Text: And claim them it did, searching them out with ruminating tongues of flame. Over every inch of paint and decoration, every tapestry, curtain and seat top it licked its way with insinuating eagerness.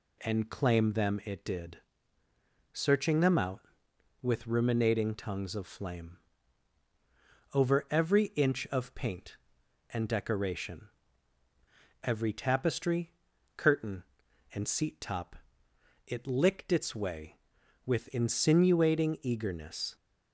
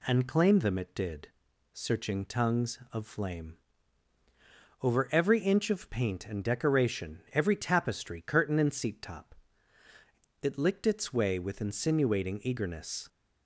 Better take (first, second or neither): first